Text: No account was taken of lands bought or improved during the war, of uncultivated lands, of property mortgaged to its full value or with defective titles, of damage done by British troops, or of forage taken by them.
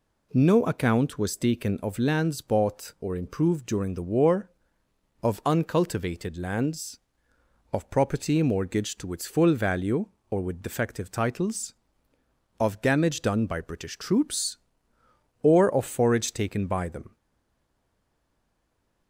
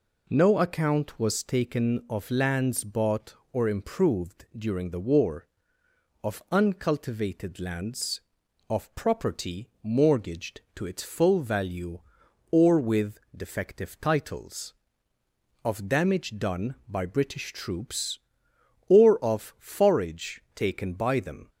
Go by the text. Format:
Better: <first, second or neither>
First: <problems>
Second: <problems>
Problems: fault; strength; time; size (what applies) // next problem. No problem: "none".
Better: second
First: stays silent after the last word; noticeable; from 17.1 s on; 1.9 s long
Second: none